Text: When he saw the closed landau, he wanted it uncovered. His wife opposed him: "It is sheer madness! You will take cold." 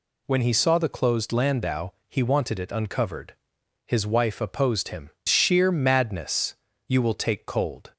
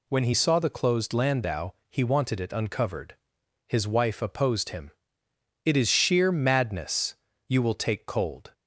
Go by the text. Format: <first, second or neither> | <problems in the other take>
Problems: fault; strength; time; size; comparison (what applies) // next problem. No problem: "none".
second | skips "It is"; at 5.1 s